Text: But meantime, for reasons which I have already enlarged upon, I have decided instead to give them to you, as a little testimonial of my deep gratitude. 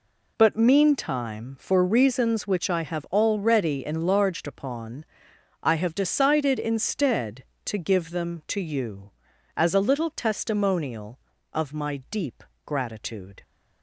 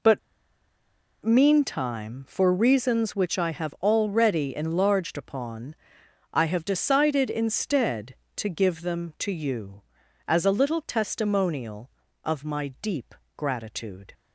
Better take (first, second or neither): first